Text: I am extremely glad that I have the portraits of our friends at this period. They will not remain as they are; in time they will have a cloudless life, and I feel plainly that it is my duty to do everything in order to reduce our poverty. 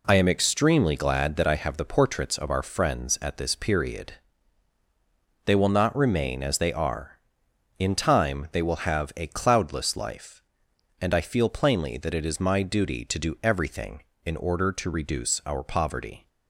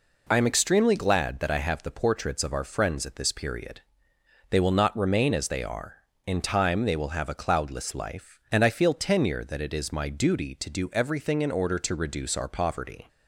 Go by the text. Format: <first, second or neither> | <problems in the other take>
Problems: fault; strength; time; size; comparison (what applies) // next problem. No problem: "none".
first | says "tenure" for "plainly"; at 8.9 s